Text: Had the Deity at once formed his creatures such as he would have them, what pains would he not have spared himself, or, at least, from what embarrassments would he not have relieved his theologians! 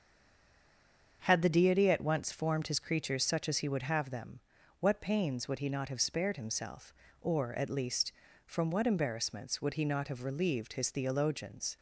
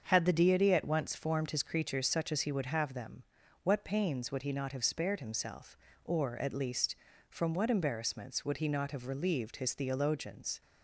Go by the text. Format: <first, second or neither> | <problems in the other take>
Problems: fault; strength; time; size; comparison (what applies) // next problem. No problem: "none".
second | stays silent before the first word; noticeable; until 1.2 s; 1.2 s long // starts louder than the rest; until 2.2 s; 7 dB; also in the second